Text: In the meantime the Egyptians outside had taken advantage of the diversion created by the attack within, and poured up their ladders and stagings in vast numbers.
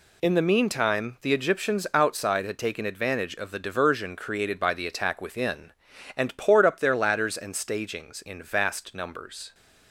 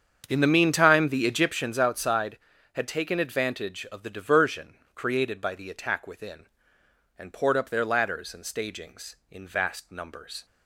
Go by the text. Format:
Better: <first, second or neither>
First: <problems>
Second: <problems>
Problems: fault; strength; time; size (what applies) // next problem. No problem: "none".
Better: first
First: none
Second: starts louder than the rest; strong; until 1.6 s; 7.5 dB // pauses between "diversion" and "created"; slight; at 4.7 s; 0.18 s long